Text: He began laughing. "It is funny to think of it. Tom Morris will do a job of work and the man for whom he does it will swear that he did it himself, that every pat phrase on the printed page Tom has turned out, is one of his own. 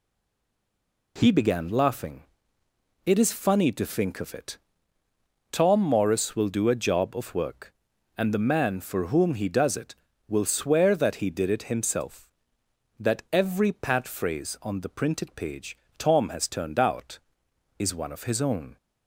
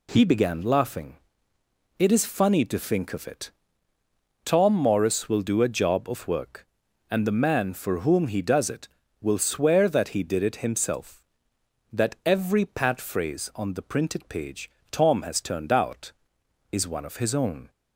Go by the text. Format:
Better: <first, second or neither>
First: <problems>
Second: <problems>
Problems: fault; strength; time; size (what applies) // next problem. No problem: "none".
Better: second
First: stays silent before the first word; until 1.1 s; 1.1 s long // pauses between "page" and "Tom"; slight; at 15.7 s; 0.22 s long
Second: pauses between "page" and "Tom"; slight; at 14.6 s; 0.22 s long